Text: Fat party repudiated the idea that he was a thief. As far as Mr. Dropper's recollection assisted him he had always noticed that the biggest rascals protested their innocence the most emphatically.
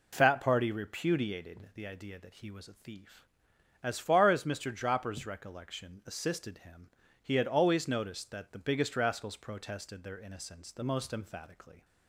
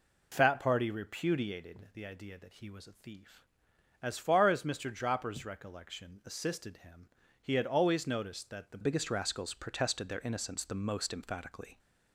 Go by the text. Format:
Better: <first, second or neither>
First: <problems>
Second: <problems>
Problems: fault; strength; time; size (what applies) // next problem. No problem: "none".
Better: first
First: pauses between "him" and "he"; at 6.8 s; 0.38 s long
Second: pauses between "him" and "he"; at 7.0 s; 0.38 s long // changes voice at "biggest"; from 8.8 s on; 2.9 s long